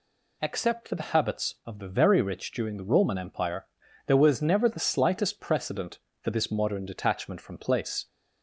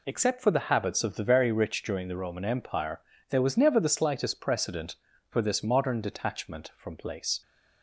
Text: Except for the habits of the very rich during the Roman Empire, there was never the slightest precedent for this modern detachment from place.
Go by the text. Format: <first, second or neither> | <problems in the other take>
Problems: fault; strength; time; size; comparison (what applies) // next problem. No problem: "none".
neither | none